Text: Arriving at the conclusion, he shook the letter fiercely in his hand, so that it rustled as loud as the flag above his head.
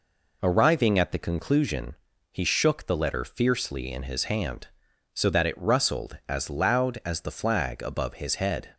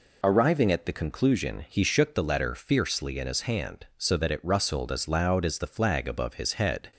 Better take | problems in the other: neither | none

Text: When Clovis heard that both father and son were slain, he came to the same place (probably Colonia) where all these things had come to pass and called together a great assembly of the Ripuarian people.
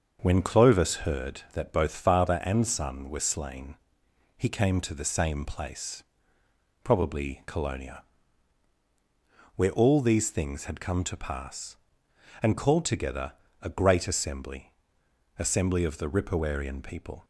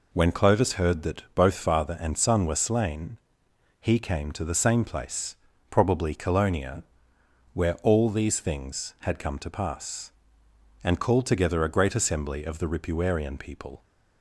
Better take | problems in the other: second | starts louder than the rest; until 1.3 s; 6.5 dB // pauses between "together" and "a"; slight; at 13.3 s; 0.30 s long // says "assembly" twice; at 15.3 s

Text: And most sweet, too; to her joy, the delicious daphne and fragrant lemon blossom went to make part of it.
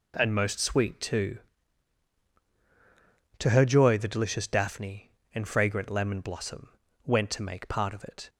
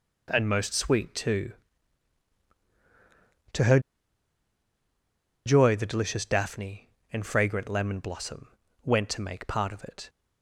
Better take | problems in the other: first | pauses between "her" and "joy"; strong; at 3.7 s; 1.6 s long // pauses between "blossom" and "went"; slight; at 8.4 s; 0.36 s long; slight in the first

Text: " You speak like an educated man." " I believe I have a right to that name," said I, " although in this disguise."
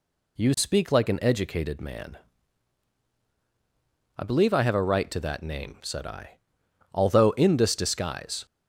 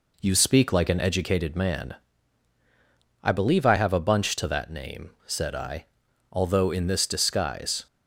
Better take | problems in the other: first | says "bunch" for "right"; at 3.9 s

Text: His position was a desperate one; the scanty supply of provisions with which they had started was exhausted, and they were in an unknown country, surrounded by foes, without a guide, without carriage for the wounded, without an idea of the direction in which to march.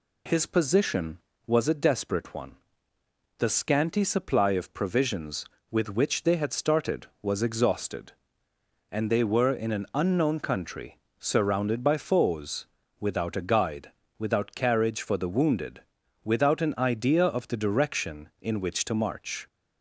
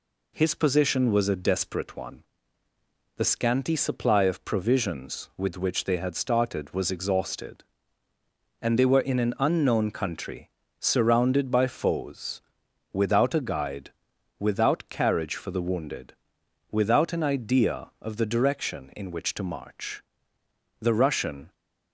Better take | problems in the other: first | goes on to say "The Russian"; noticeable; from 20.8 s on; 0.72 s long

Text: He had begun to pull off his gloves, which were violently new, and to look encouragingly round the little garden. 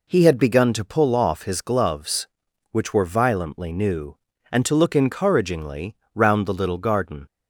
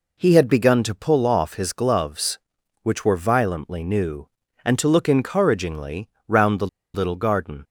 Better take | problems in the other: first | pauses between "encouragingly" and "round"; slight; at 6.0 s; 0.18 s long; slight in the first // pauses between "the" and "little"; slight; at 6.6 s; 0.27 s long

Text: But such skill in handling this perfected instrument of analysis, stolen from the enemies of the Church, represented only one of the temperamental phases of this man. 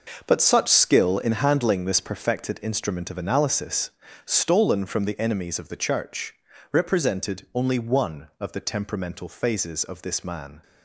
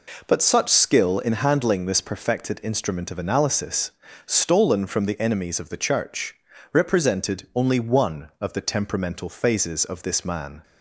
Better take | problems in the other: second | gets quieter; strong; throughout; 11.5 dB

